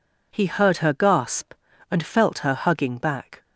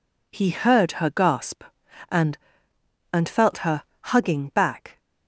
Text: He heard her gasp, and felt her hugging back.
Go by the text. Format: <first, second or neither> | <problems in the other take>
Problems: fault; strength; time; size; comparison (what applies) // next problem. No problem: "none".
first | says "and" twice; at 3.1 s // pauses between "her" and "hugging"; slight; at 3.8 s; 0.18 s long